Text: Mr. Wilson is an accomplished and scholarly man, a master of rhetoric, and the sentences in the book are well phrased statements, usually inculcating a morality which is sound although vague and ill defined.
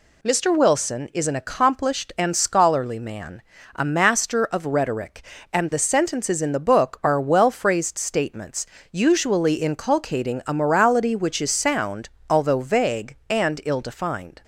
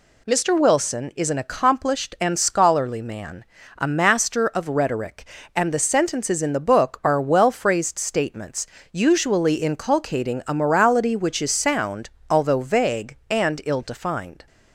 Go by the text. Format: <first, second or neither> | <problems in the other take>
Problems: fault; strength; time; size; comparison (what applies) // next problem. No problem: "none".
neither | pauses between "sound" and "although"; slight; the same in both